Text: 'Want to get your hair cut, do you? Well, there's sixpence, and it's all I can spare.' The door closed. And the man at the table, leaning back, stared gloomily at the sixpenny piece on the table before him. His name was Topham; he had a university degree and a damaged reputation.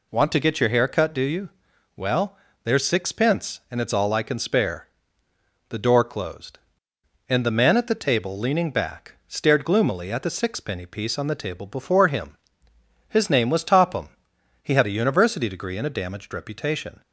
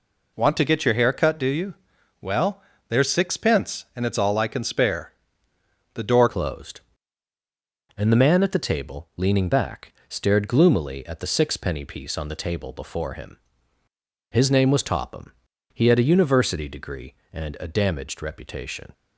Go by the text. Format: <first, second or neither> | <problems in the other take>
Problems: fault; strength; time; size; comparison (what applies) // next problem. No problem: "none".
first | changes voice at "closed"; from 6.2 s on; 12.7 s long